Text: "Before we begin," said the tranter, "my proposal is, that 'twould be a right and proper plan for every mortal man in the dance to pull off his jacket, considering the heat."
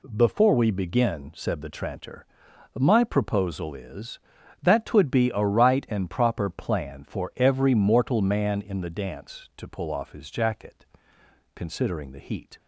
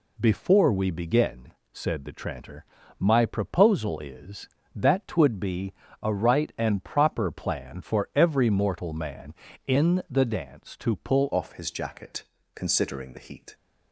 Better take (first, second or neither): first